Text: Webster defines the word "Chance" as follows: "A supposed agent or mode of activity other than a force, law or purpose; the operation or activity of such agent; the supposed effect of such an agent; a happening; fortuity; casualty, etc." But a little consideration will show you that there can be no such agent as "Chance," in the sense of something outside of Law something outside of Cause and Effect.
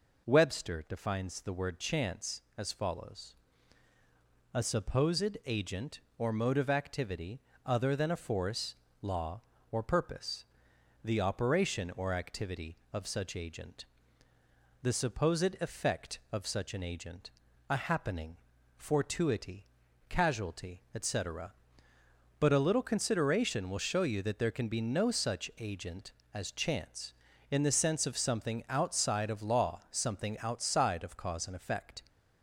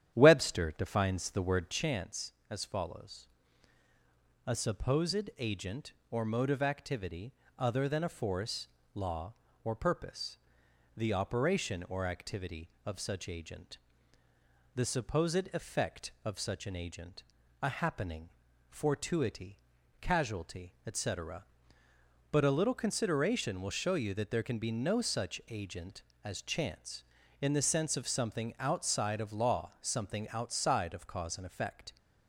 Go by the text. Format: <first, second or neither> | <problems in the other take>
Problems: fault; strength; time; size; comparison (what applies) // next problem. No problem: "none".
first | starts louder than the rest; strong; until 1.9 s; 10 dB // pauses between "activity" and "other"; slight; at 7.3 s; 0.24 s long; slight in the first